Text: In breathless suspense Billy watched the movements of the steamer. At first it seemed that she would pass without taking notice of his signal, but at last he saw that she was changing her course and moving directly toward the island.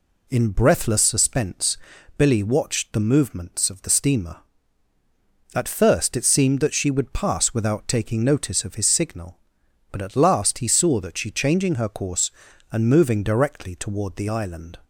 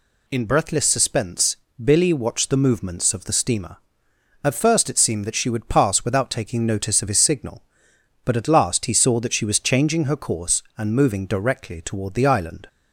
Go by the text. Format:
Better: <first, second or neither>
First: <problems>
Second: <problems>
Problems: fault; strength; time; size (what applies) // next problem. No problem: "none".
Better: second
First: pauses between "suspense" and "Billy"; at 1.7 s; 0.38 s long // skips "was"; at 11.2 s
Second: pauses between "suspense" and "Billy"; slight; at 1.5 s; 0.28 s long